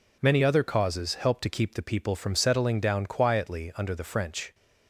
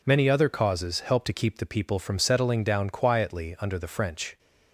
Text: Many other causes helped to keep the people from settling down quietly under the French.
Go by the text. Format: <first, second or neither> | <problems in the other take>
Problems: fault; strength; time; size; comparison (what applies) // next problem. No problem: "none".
neither | none